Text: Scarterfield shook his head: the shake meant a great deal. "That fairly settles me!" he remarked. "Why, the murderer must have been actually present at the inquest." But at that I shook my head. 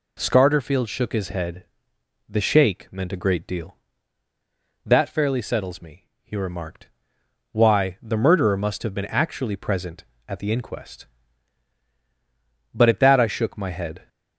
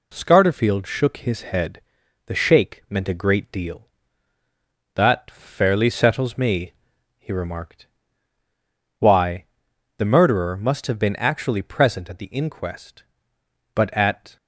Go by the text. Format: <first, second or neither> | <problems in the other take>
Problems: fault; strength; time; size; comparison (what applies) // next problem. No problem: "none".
first | stops before "that I shook my head"; at 14.3 s